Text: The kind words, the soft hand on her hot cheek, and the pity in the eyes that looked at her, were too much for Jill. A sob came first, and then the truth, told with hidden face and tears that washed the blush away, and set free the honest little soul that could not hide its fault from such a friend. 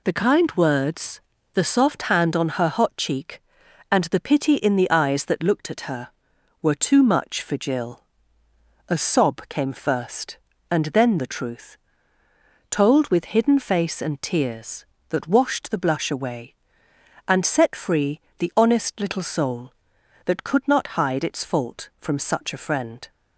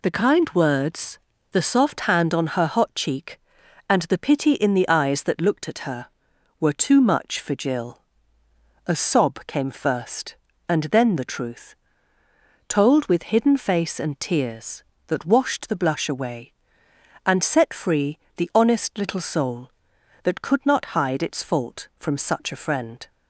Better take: neither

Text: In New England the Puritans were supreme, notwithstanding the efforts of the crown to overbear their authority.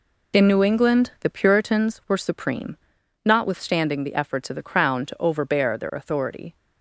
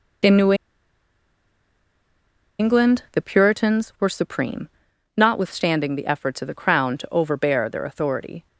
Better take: first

